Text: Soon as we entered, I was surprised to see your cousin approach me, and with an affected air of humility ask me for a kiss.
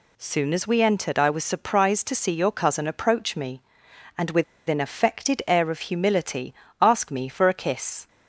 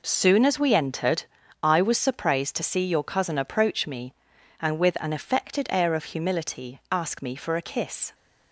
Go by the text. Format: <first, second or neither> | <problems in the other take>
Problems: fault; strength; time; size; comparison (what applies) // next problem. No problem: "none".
second | pauses between "with" and "an"; slight; at 4.4 s; 0.25 s long // pauses between "humility" and "ask"; slight; at 6.5 s; 0.26 s long